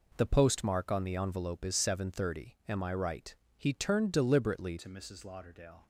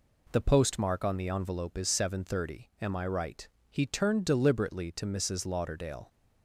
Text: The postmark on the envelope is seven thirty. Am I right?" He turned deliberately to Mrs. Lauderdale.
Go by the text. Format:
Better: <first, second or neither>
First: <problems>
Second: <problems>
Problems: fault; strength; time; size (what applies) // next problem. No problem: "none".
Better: second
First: changes voice at "to"; from 4.7 s on; 1.1 s long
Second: none